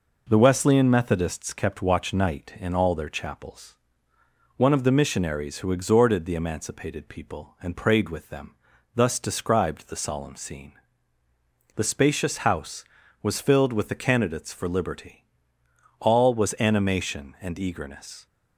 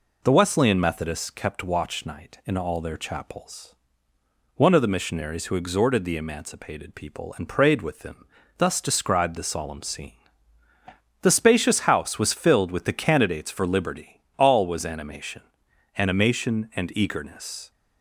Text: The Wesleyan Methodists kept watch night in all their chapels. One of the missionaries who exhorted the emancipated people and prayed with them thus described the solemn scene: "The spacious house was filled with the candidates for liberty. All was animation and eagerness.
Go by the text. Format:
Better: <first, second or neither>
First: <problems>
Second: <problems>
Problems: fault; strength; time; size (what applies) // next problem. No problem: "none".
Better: first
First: pauses between "them" and "thus"; at 8.5 s; 0.40 s long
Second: pauses between "them" and "thus"; slight; at 8.2 s; 0.32 s long // says "animation" twice; at 15.9 s